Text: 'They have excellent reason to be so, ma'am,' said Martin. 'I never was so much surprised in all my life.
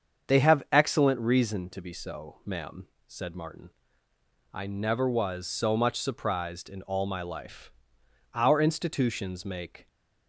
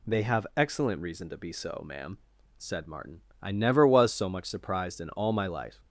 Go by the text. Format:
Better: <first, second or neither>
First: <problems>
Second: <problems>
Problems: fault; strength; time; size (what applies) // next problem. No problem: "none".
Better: second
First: starts louder than the rest; until 1.3 s; 7 dB // goes on to say "Our institutions make"; from 8.3 s on; 1.5 s long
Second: none